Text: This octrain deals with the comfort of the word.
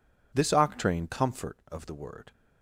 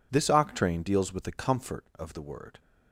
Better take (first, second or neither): second